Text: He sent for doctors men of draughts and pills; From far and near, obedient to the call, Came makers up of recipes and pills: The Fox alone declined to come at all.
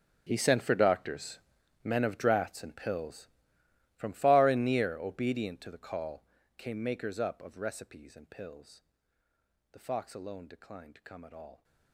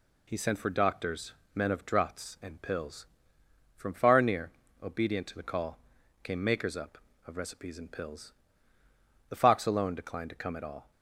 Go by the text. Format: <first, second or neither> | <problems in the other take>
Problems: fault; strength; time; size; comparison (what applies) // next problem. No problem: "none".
second | gets quieter; strong; throughout; 19 dB // pauses between "doctors" and "men"; noticeable; at 1.3 s; 0.46 s long; slight in the second